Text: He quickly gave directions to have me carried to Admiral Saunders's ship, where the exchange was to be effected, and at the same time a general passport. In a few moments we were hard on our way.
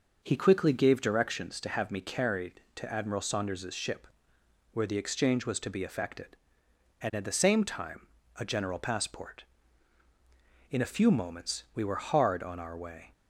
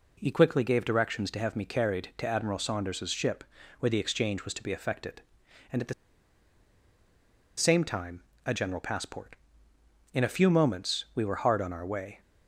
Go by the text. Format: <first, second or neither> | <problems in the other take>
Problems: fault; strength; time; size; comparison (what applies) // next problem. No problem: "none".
first | pauses between "the" and "same"; strong; at 5.9 s; 1.6 s long // pauses between "time" and "a"; slight; at 8.2 s; 0.24 s long; slight in the first